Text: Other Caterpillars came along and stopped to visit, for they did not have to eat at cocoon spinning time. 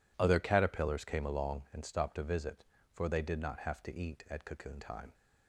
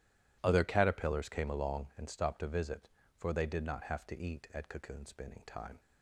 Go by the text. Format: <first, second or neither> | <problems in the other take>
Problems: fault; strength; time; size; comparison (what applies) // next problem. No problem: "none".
second | skips "spinning"; at 4.8 s